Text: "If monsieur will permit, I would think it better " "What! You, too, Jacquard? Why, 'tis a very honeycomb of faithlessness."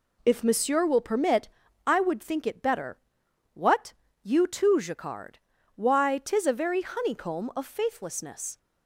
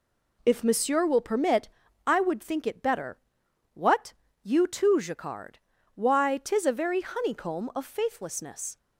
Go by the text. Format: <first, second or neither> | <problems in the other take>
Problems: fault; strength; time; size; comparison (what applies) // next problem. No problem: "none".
neither | none